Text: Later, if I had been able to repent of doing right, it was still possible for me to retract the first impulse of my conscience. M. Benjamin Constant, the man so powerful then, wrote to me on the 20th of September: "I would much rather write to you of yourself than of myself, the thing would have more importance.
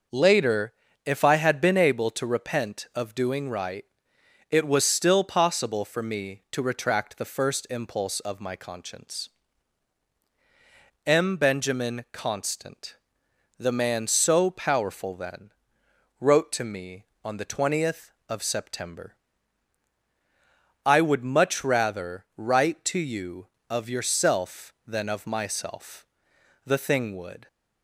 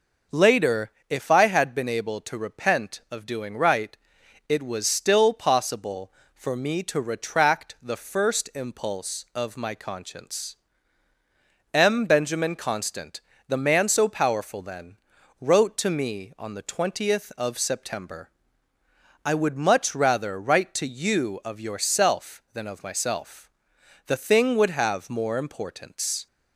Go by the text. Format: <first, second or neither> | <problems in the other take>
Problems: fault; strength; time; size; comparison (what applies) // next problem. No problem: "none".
second | stops before "have more importance"; at 27.4 s